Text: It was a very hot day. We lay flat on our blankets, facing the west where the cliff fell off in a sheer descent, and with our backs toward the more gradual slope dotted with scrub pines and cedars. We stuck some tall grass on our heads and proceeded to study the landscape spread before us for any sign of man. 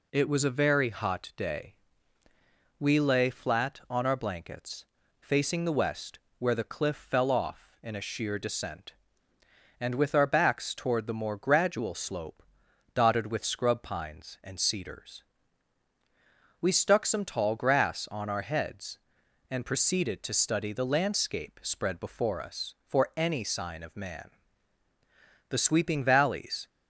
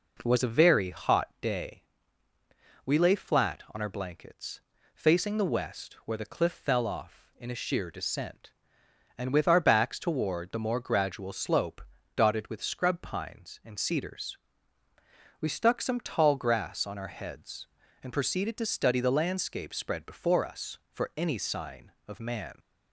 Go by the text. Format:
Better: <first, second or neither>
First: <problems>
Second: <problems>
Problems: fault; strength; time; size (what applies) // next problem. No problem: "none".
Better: second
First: pauses between "west" and "where"; slight; at 6.1 s; 0.18 s long // pauses between "slope" and "dotted"; noticeable; at 12.4 s; 0.52 s long // goes on to say "The sweeping valleys"; noticeable; from 25.4 s on; 1.1 s long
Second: pauses between "slope" and "dotted"; slight; at 11.8 s; 0.34 s long